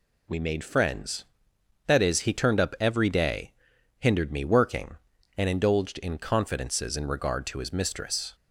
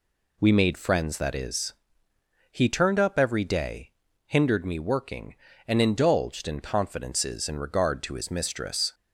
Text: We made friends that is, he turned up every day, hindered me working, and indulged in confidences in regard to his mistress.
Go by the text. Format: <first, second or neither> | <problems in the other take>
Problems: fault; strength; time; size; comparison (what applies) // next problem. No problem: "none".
neither | none